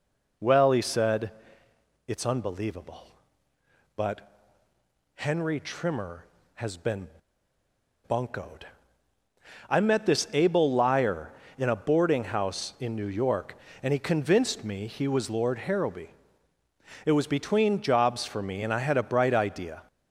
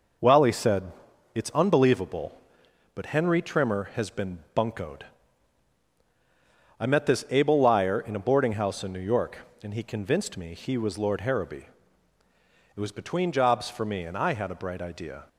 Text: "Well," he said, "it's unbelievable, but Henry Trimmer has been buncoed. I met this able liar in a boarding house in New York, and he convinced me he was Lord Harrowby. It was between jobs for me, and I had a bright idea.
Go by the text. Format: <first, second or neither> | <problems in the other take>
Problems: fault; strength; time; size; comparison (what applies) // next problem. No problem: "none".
second | pauses between "but" and "Henry"; noticeable; at 4.3 s; 0.84 s long // pauses between "been" and "buncoed"; at 7.0 s; 0.99 s long